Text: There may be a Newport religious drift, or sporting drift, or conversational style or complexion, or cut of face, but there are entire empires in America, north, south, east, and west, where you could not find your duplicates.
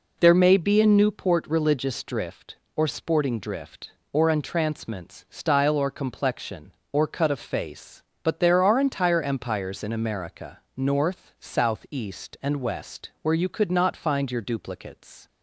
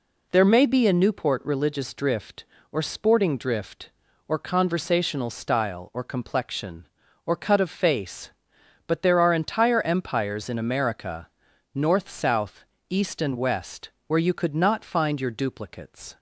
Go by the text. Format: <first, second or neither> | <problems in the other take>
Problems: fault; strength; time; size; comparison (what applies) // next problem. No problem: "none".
second | says "entrancements" for "conversational"; at 4.2 s